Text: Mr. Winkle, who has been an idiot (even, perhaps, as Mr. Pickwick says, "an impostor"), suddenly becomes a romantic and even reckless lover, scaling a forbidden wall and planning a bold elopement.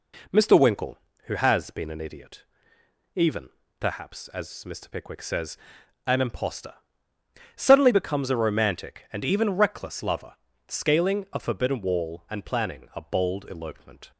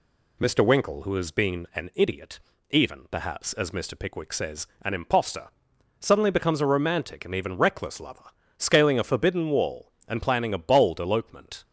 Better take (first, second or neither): neither